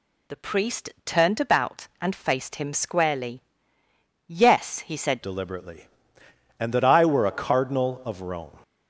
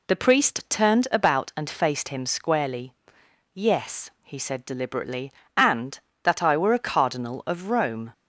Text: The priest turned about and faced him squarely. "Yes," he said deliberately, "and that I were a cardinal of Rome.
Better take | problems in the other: second | changes voice at "deliberately"; from 5.2 s on; 3.3 s long

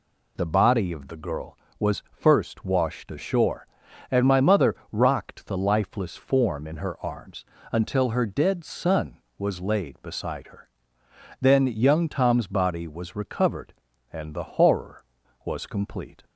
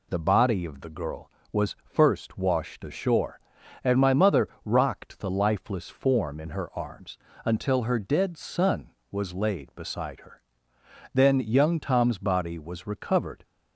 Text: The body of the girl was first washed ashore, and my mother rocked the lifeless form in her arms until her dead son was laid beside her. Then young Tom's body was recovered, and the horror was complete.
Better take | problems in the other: first | pauses between "mother" and "rocked"; slight; at 4.4 s; 0.18 s long; slight in the first // pauses between "arms" and "until"; slight; at 7.1 s; 0.30 s long; slight in the first // stops before "and the horror was complete"; at 13.4 s

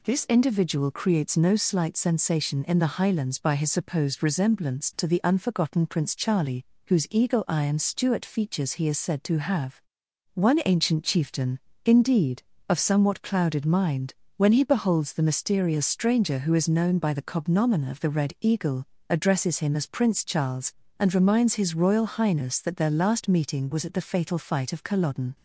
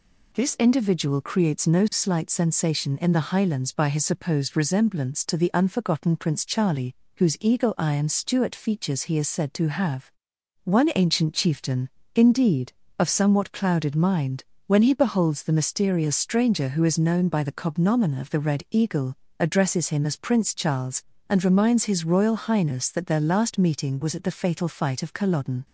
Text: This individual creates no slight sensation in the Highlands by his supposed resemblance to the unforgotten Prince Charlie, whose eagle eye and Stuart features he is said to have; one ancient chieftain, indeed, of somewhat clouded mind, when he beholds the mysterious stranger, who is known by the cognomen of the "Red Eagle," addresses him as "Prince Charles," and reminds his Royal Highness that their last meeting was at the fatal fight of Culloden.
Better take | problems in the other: neither | none

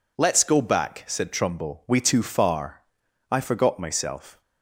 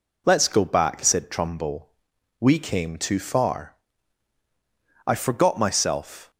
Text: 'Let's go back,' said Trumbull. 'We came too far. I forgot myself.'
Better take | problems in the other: second | skips "came"; at 2.0 s

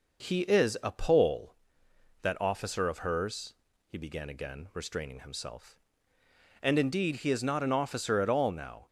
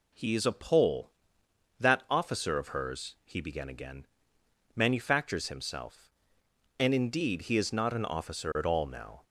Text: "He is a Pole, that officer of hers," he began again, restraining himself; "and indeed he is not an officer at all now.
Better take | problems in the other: first | says "manufactures" for "restraining"; at 4.7 s

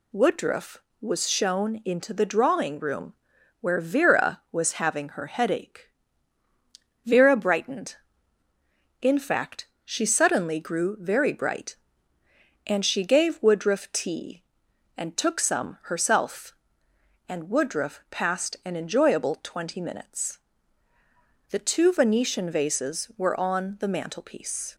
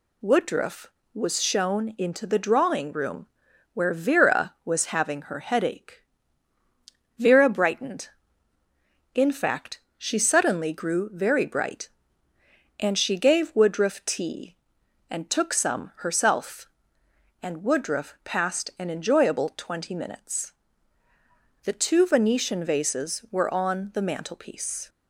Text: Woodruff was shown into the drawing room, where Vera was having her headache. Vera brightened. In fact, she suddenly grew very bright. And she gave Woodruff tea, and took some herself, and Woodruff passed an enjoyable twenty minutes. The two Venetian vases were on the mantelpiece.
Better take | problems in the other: neither | none

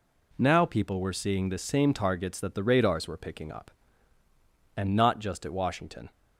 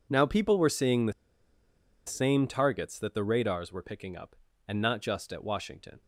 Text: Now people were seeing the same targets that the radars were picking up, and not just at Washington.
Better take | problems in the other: first | pauses between "the" and "same"; noticeable; at 1.1 s; 0.94 s long

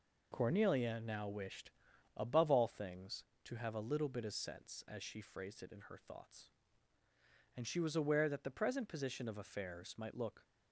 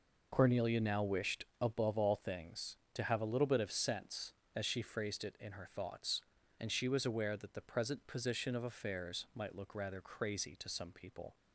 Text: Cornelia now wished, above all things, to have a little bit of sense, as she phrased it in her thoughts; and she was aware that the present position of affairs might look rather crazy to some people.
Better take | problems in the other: second | stops before "rather crazy to some people"; at 10.4 s

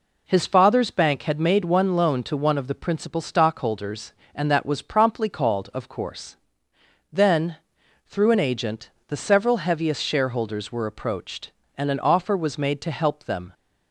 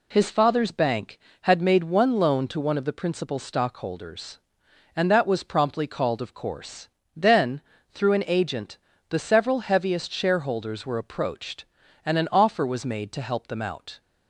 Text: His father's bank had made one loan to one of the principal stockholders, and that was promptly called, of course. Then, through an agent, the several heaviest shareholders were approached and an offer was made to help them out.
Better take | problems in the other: second | stops before "out"; at 13.5 s

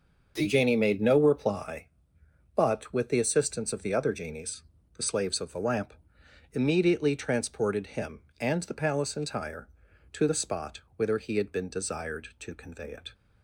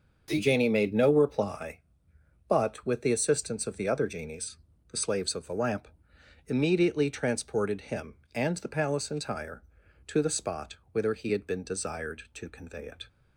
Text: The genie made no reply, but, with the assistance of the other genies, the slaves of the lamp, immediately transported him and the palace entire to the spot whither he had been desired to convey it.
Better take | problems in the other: neither | starts louder than the rest; noticeable; the same in both // pauses between "spot" and "whither"; slight; the same in both

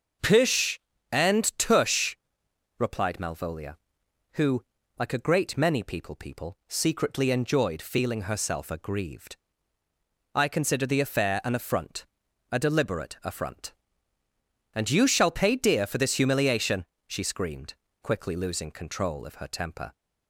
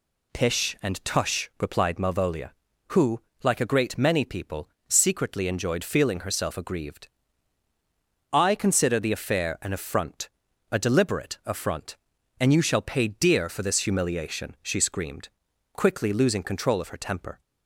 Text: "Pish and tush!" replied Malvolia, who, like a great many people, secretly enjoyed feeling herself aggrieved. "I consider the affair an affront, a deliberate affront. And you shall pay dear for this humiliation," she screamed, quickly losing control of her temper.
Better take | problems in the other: second | starts louder than the rest; until 1.5 s; 6.5 dB // says "people" twice; at 6.1 s

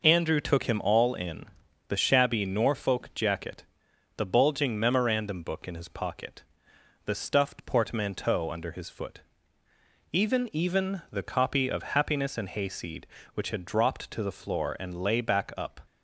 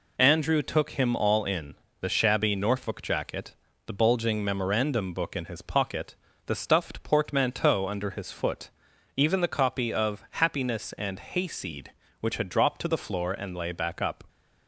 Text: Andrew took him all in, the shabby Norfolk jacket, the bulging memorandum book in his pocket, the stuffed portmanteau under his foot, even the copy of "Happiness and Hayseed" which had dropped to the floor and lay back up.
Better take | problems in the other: second | says "even" twice; at 10.5 s

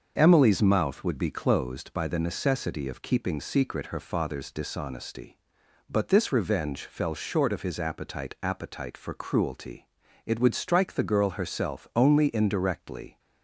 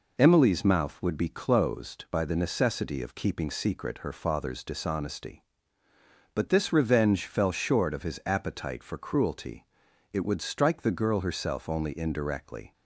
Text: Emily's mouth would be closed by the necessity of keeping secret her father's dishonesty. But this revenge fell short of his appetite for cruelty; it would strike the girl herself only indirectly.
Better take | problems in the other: second | starts louder than the rest; until 1.1 s; 6.5 dB // says "appetite" twice; at 8.4 s

